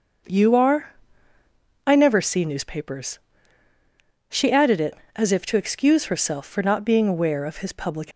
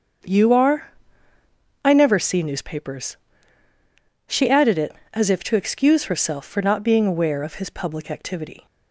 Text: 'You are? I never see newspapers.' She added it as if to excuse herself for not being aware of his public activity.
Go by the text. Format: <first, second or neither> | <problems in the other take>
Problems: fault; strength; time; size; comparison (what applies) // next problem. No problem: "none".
second | starts louder than the rest; until 2.2 s; 6.5 dB; strong in the second // stops before "activity"; at 8.1 s